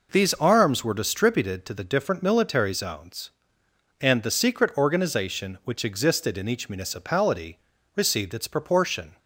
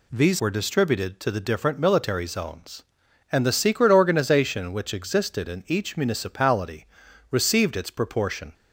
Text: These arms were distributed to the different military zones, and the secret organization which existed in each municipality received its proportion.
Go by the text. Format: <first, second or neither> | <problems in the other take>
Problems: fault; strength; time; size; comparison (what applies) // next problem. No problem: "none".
first | skips "arms"; at 0.3 s // pauses between "municipality" and "received"; at 6.8 s; 0.42 s long; slight in the first